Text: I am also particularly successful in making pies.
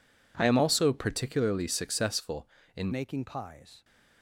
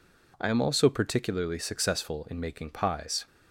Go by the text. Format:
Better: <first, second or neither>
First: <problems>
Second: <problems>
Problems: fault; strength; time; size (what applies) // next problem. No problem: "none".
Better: second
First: changes voice at "making"; from 2.9 s on; 0.9 s long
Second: none